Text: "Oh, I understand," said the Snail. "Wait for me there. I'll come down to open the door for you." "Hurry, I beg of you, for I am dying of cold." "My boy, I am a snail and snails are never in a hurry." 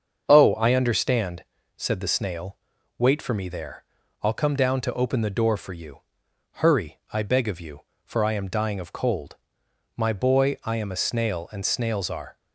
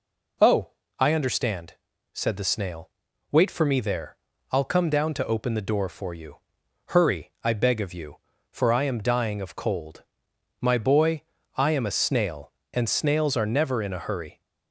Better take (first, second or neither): second